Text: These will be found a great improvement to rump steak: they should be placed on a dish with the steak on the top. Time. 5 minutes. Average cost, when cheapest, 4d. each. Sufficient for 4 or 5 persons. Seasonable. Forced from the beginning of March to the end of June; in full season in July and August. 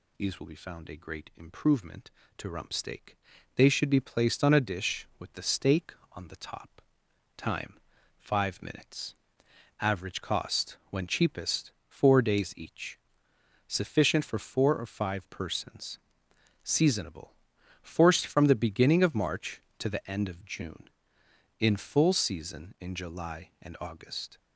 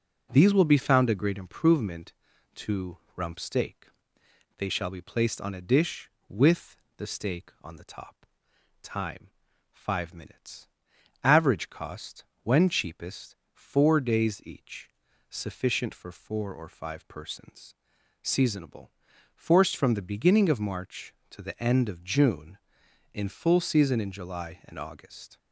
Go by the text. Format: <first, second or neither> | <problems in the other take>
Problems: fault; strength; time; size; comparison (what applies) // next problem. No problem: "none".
first | pauses between "to" and "rump"; slight; at 2.9 s; 0.18 s long // says "shall" for "should"; at 4.6 s // pauses between "with" and "the"; slight; at 6.7 s; 0.22 s long